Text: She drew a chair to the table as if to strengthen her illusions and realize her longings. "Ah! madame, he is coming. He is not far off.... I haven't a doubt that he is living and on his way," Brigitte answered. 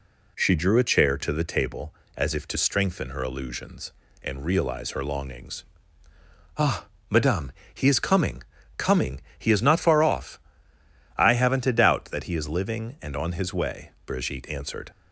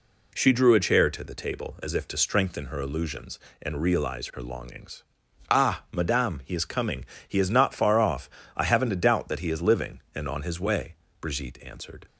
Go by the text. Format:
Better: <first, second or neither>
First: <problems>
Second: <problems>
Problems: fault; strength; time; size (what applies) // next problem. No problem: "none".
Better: second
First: says "coming" twice; at 8.7 s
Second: none